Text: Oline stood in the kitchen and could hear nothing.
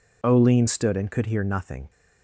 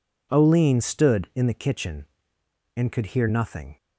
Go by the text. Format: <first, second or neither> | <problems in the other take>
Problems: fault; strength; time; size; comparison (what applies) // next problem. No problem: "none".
second | skips "in the kitchen"; at 0.9 s